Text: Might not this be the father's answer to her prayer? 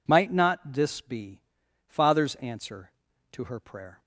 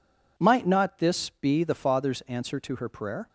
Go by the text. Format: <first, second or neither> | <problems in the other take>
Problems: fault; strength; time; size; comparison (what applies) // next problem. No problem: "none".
second | skips "the"; at 1.6 s